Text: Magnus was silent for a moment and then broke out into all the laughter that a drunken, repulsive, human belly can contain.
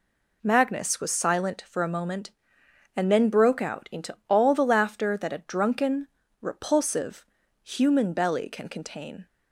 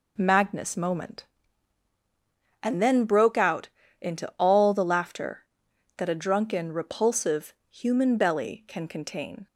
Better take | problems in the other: first | skips "was silent for a"; at 0.7 s // pauses between "out" and "into"; slight; at 3.6 s; 0.32 s long

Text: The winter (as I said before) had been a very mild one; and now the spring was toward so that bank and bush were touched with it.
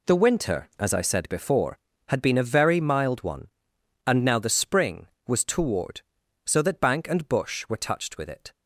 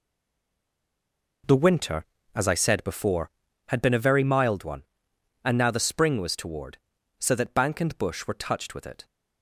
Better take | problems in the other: first | stays silent before the first word; noticeable; until 1.4 s; 1.4 s long

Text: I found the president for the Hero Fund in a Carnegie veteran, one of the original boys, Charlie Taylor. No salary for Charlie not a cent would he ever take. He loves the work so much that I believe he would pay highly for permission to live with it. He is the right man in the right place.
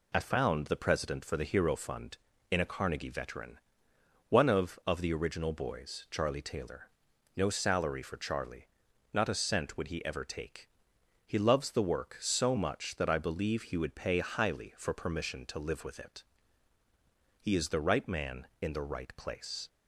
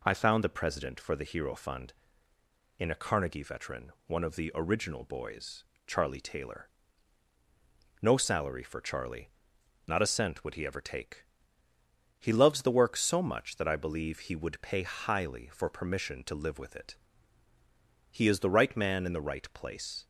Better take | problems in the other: second | says "of" twice; at 4.8 s // pauses between "Charlie" and "not"; noticeable; at 8.6 s; 0.48 s long; noticeable in the second

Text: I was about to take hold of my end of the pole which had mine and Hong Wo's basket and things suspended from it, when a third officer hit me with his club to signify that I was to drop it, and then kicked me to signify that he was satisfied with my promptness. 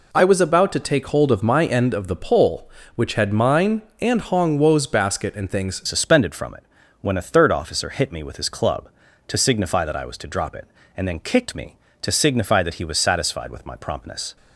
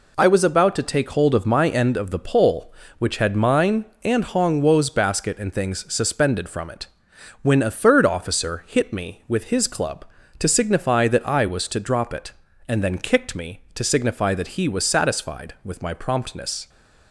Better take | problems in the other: second | changes voice at "suspended"; from 5.8 s on; 8.5 s long

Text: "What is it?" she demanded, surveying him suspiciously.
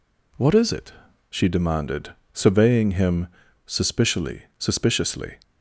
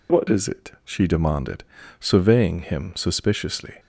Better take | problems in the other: second | pauses between "him" and "suspiciously"; at 3.2 s; 0.40 s long // says "suspiciously" twice; at 4.5 s

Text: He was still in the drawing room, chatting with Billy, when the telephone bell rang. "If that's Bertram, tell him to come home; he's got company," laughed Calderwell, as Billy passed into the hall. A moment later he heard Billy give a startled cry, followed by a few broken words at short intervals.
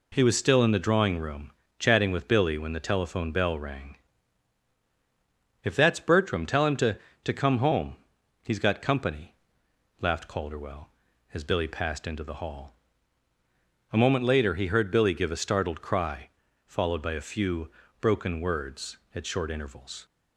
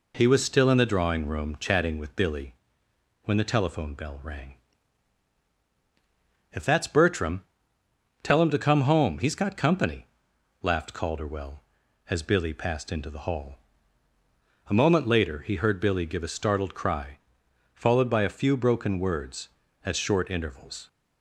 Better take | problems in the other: second | says "to" twice; at 7.2 s // pauses between "few" and "broken"; slight; at 17.7 s; 0.28 s long

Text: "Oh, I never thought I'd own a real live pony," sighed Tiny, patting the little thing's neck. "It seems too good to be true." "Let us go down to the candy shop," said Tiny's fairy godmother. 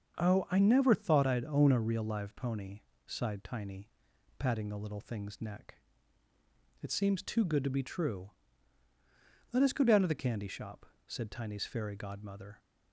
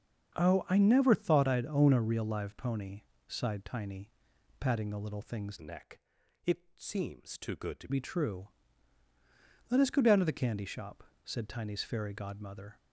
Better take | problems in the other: first | starts louder than the rest; until 1.3 s; 6.5 dB; also in the first // changes voice from "neck" to "to"; from 5.6 to 7.8 s; 2.2 s long

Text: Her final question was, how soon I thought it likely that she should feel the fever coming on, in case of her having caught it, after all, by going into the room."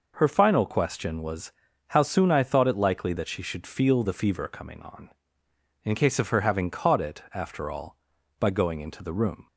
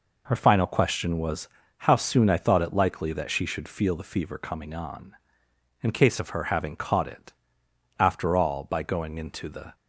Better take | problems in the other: first | stops before "room"; at 9.7 s

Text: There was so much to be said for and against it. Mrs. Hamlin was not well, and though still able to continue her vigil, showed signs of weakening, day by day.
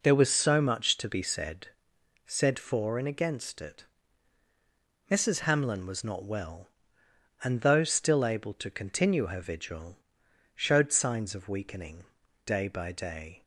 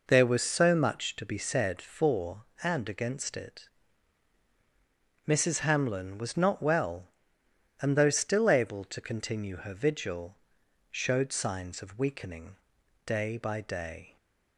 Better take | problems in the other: second | says "said" twice; at 2.2 s

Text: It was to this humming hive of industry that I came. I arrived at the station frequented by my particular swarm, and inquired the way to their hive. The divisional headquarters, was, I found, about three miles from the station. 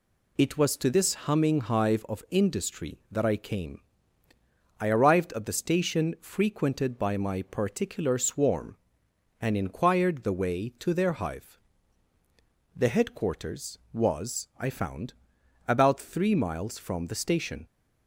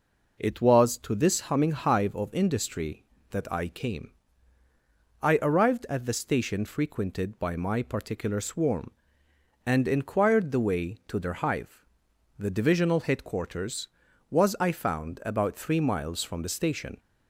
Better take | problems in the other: second | skips "divisional"; at 12.8 s

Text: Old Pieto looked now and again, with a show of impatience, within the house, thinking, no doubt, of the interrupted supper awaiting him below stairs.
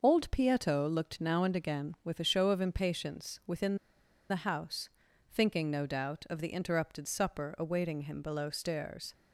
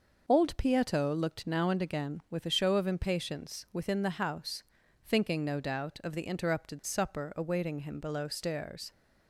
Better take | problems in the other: second | pauses between "within" and "the"; noticeable; at 3.7 s; 0.53 s long

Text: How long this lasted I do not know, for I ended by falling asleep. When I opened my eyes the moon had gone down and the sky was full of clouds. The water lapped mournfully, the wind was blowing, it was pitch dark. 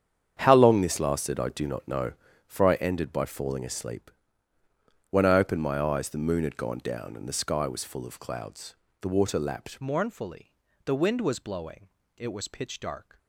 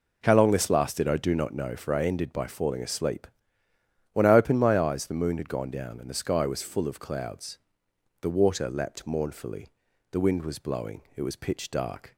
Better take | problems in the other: second | starts louder than the rest; strong; until 1.4 s; 8 dB // changes voice at "mournfully"; from 9.8 s on; 3.3 s long

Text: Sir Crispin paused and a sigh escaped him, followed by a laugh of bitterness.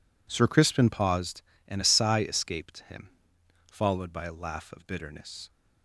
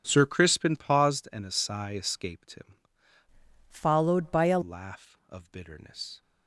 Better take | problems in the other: first | starts louder than the rest; strong; until 1.0 s; 8 dB // changes voice from "followed" to "a"; from 3.6 to 4.5 s; 0.9 s long

